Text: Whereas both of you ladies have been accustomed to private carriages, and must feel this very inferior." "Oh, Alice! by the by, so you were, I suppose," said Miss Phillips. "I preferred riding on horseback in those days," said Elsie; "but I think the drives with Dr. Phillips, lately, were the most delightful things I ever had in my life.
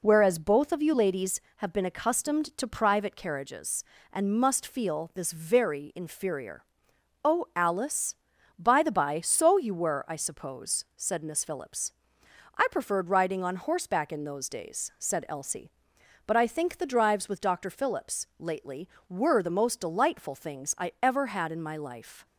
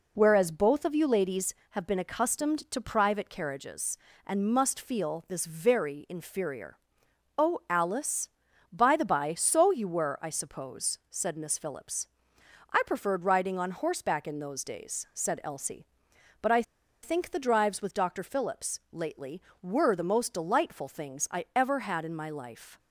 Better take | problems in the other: first | pauses between "I" and "think"; at 16.6 s; 0.40 s long

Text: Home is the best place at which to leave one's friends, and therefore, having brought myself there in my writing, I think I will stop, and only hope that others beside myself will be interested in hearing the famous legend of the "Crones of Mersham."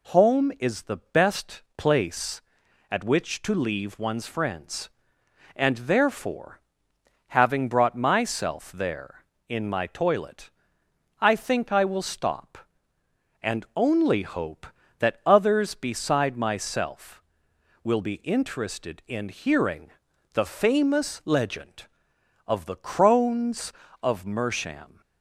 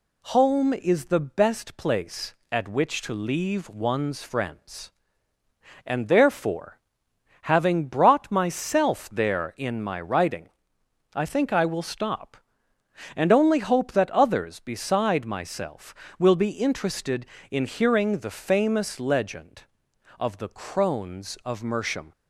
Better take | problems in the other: second | says "toilet" for "writing"; at 9.8 s // pauses between "hearing" and "the"; at 19.9 s; 0.42 s long

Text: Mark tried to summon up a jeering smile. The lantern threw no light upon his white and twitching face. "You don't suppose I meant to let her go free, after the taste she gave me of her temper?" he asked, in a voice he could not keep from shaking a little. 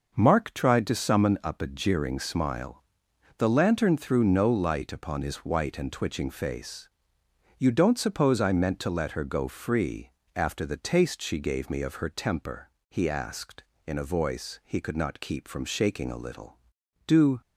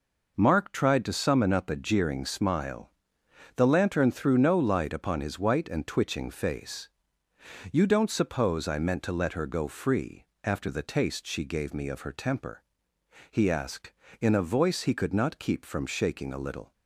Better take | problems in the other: second | goes on to say "Do"; slight; from 17.0 s on; 0.34 s long

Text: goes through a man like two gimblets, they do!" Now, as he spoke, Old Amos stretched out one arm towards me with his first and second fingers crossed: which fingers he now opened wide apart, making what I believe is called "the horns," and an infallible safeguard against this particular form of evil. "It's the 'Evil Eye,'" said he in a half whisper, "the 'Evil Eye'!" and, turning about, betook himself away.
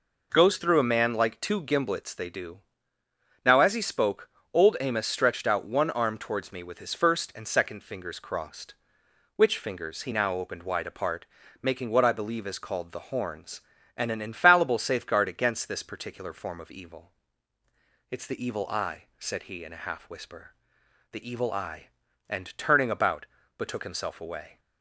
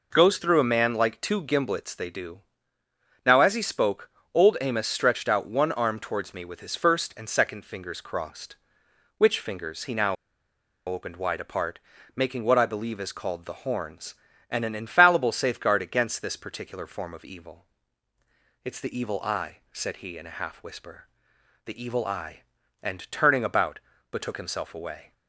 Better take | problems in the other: first | pauses between "now" and "opened"; noticeable; at 10.1 s; 0.73 s long

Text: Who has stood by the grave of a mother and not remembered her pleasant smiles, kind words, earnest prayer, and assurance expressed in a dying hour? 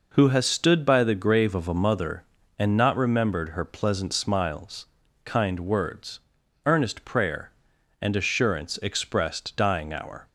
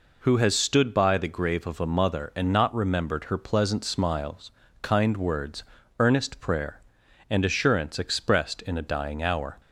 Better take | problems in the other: second | skips "in a"; at 9.5 s

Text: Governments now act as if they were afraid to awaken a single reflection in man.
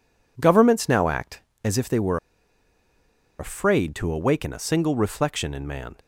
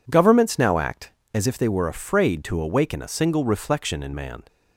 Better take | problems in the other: second | pauses between "were" and "afraid"; at 2.1 s; 1.2 s long

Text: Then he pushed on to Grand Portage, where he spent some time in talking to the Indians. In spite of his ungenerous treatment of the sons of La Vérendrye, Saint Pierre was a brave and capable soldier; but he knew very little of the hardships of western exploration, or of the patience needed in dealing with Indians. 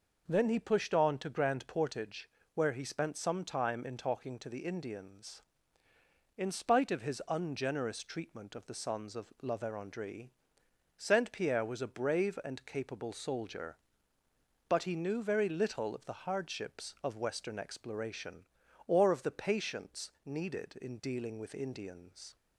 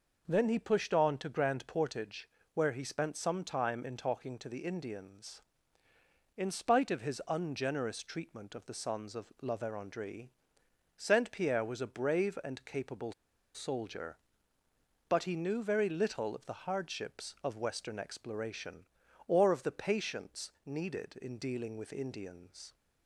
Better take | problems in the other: first | pauses between "capable" and "soldier"; at 13.1 s; 0.43 s long // pauses between "patience" and "needed"; slight; at 20.4 s; 0.16 s long; slight in the first

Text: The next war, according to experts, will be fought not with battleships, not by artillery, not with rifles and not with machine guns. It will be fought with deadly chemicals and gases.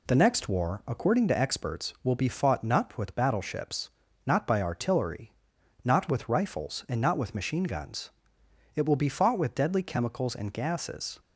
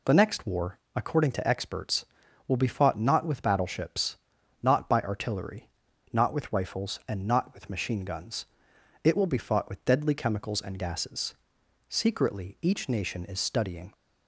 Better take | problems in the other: first | goes on to say "Secretly each nation is studying"; strong; from 11.8 s on; 2.0 s long

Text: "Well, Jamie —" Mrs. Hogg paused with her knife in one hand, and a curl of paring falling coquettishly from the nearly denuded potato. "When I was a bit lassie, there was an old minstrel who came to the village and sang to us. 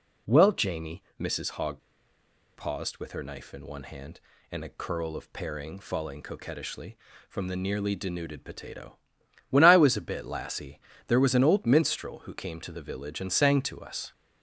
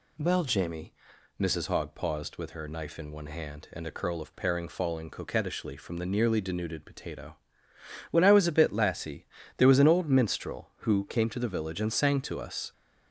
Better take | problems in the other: second | pauses between "Hogg" and "paused"; noticeable; at 1.8 s; 0.75 s long

